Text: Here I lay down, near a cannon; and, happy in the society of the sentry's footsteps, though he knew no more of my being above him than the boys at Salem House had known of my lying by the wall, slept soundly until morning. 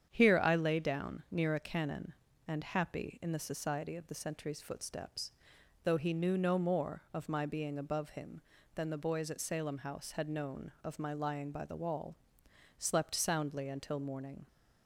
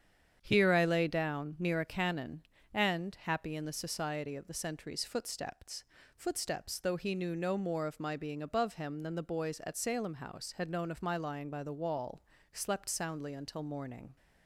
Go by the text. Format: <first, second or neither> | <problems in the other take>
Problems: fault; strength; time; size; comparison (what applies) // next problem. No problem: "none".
first | starts louder than the rest; strong; until 1.4 s; 8.5 dB; strong in the first // says "footsteps" twice; at 6.1 s